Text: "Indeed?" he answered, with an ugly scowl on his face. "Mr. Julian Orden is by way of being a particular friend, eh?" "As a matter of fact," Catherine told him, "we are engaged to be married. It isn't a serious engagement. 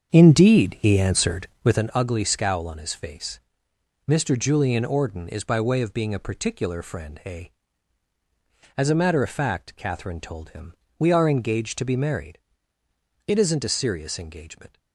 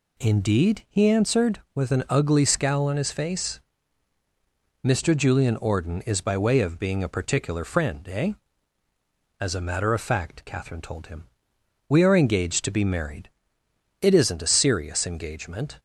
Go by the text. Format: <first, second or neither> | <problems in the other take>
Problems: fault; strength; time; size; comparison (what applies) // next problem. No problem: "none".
second | starts louder than the rest; strong; until 1.9 s; 7 dB